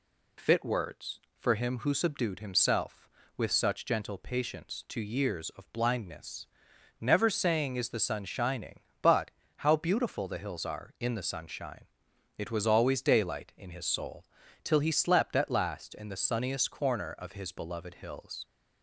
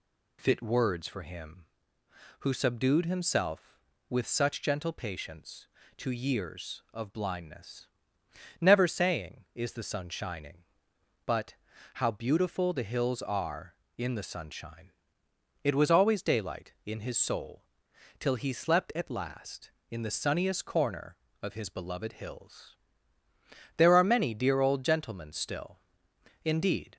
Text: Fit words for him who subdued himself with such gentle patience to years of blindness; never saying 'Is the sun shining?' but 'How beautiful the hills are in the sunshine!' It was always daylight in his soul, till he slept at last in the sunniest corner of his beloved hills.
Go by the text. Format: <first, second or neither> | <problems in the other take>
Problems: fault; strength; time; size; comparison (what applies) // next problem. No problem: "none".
first | pauses between "but" and "How"; at 11.5 s; 0.40 s long; slight in the first // goes on to say "There are many dear old gentlemen still indeed"; strong; from 23.7 s on; 3.2 s long